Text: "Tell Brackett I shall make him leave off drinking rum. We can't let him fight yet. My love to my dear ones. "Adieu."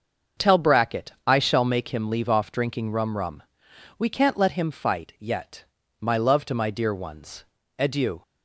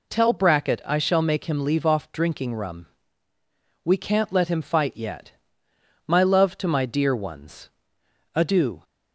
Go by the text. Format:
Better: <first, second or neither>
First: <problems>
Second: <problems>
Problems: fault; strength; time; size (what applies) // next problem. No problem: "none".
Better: second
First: starts louder than the rest; until 1.5 s; 6.5 dB // says "rum" twice; at 3.1 s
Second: none